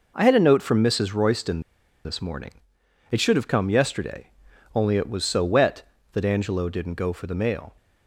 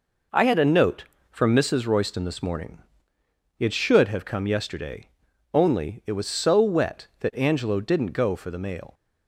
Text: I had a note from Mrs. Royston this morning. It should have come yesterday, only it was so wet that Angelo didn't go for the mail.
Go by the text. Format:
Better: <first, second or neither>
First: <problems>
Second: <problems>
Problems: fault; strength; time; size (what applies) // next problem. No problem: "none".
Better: second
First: pauses between "Royston" and "this"; at 1.6 s; 0.43 s long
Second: none